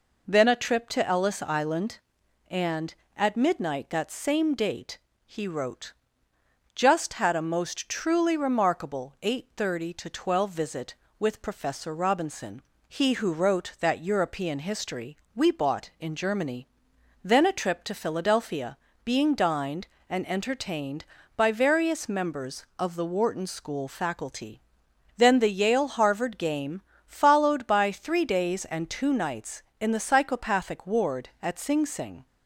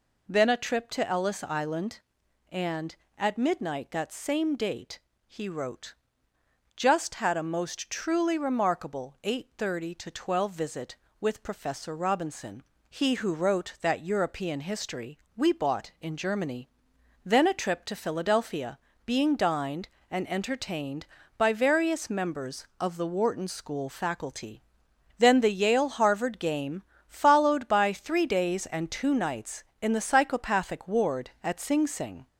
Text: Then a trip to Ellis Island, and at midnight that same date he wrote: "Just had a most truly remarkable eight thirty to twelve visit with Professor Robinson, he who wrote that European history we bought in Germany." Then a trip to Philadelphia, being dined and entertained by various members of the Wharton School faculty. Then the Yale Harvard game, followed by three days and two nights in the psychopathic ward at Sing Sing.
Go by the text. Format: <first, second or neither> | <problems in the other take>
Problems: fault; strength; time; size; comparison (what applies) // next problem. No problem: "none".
first | gets louder; slight; throughout; 2.5 dB // pauses between "date" and "he"; slight; at 4.9 s; 0.26 s long; slight in the first // pauses between "history" and "we"; slight; at 15.1 s; 0.20 s long; slight in the first